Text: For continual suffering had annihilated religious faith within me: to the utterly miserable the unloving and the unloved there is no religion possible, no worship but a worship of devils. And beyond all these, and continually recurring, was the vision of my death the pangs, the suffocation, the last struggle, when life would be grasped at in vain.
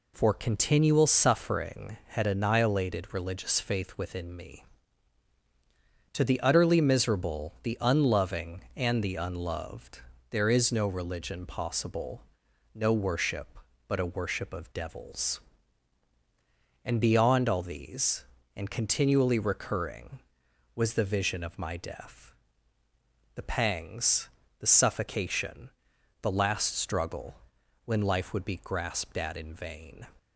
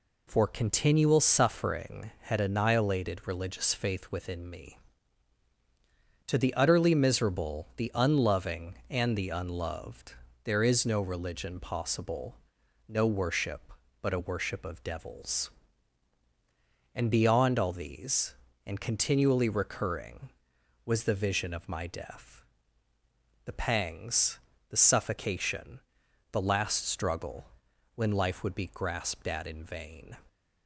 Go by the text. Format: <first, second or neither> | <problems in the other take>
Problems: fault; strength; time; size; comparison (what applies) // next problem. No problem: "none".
neither | pauses between "unloved" and "there"; slight; the same in both // pauses between "death" and "the"; the same in both